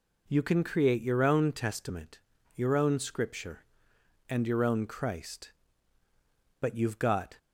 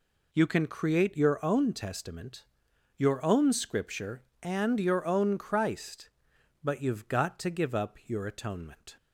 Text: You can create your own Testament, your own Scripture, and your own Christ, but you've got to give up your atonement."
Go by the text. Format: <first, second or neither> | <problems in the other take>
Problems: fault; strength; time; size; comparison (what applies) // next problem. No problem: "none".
second | stops before "to give up your atonement"; at 7.3 s